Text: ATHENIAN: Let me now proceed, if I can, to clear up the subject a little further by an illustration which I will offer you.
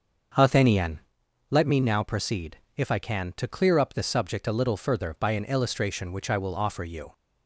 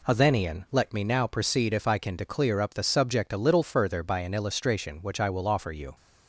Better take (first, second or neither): second